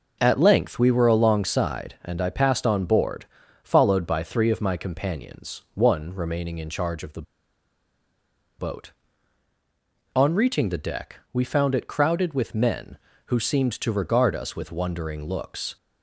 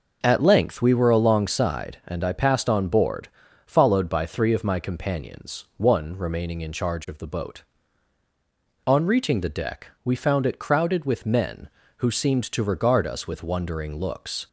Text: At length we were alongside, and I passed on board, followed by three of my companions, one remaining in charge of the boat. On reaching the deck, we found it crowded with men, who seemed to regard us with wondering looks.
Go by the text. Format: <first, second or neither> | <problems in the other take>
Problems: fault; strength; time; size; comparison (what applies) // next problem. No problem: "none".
second | pauses between "the" and "boat"; strong; at 7.2 s; 1.3 s long